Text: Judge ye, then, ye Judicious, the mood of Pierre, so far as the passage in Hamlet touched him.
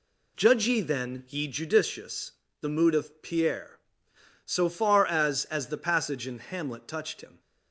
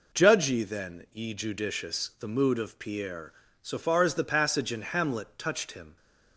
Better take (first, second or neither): second